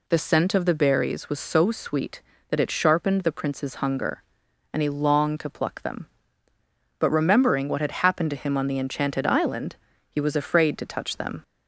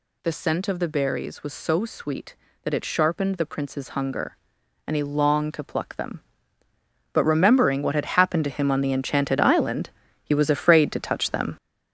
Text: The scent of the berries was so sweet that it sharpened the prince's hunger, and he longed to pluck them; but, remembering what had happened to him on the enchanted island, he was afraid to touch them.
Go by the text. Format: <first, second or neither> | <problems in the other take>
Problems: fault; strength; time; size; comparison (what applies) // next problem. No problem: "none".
first | gets louder; throughout; 7 dB